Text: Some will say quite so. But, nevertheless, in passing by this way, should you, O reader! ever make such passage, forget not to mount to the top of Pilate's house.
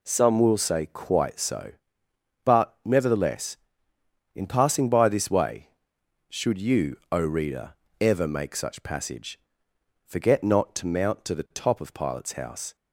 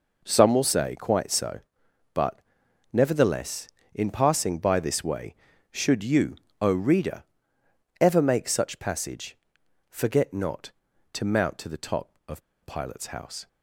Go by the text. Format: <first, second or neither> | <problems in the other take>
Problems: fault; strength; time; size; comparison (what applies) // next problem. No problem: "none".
first | pauses between "of" and "Pilate's"; slight; at 12.4 s; 0.26 s long